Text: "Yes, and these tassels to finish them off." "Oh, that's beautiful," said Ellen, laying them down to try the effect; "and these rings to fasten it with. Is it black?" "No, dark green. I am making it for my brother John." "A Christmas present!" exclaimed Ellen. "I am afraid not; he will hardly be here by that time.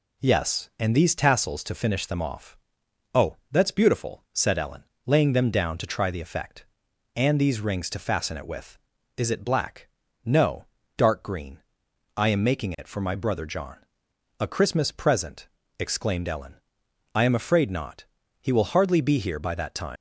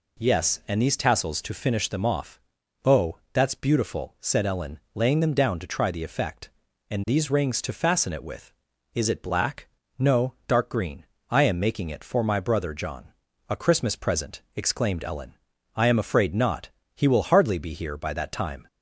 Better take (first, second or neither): second